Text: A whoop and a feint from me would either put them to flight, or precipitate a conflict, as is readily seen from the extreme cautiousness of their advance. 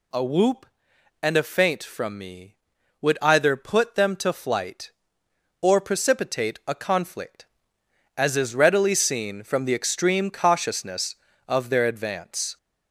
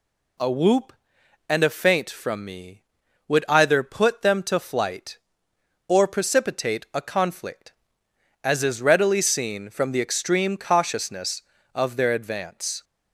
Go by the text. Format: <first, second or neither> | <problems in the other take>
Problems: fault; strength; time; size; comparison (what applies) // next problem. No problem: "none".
second | gets louder; slight; throughout; 3 dB